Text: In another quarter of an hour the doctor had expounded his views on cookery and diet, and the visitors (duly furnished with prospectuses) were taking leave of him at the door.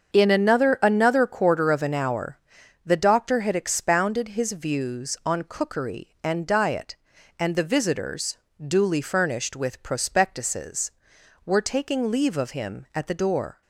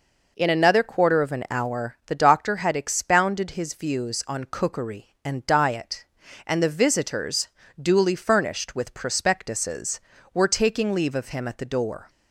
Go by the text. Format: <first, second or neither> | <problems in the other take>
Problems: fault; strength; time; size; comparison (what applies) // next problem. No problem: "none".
second | starts louder than the rest; until 1.1 s; 7 dB // says "another" twice; at 0.8 s // pauses between "hour" and "the"; noticeable; at 2.3 s; 0.48 s long